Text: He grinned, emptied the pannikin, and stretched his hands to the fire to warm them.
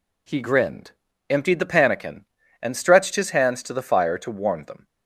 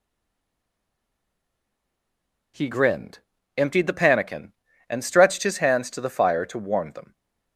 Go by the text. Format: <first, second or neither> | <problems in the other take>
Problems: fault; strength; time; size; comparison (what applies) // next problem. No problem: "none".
first | stays silent before the first word; strong; until 2.5 s; 2.5 s long